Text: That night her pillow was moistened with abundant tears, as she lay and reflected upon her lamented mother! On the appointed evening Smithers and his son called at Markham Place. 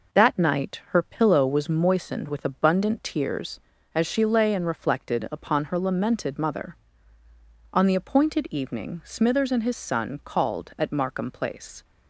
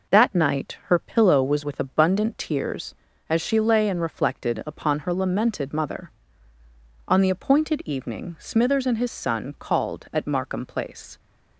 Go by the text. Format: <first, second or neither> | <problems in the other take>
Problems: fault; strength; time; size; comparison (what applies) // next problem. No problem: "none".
first | skips "moistened"; at 1.6 s